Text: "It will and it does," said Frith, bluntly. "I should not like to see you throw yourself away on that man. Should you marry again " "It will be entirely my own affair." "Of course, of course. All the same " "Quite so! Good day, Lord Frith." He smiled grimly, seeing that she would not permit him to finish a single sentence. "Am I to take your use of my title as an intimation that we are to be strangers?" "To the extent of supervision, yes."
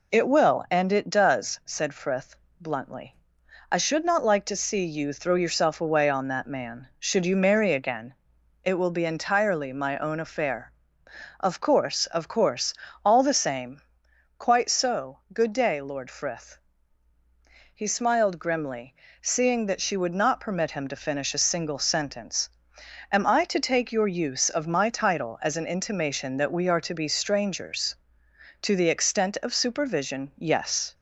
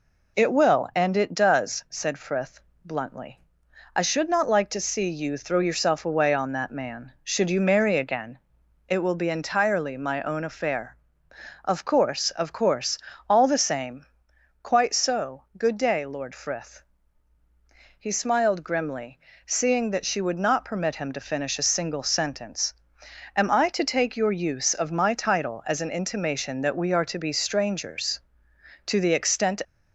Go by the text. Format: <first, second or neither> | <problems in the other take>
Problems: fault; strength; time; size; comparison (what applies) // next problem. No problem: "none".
first | stops before "of supervision yes"; at 29.6 s